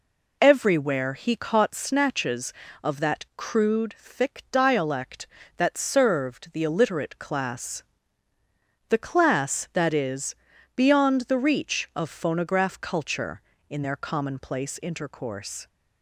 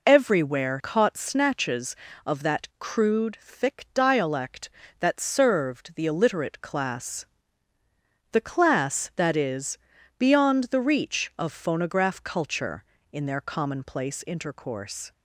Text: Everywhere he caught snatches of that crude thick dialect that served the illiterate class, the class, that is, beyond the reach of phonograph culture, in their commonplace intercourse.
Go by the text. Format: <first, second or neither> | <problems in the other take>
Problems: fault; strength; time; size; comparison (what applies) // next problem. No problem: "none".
first | skips "he"; at 0.7 s